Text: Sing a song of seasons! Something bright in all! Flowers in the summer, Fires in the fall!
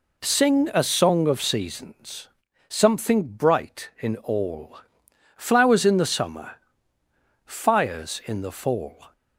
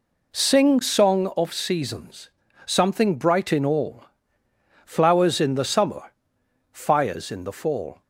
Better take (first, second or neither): first